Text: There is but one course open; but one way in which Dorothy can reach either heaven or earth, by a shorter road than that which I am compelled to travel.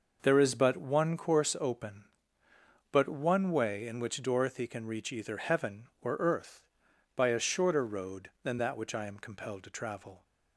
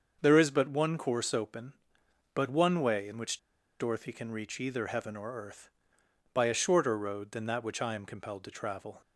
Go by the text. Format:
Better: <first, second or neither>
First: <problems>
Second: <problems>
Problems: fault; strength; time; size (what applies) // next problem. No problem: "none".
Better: first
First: none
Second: starts louder than the rest; until 1.2 s; 6.5 dB // pauses between "which" and "Dorothy"; at 3.3 s; 0.41 s long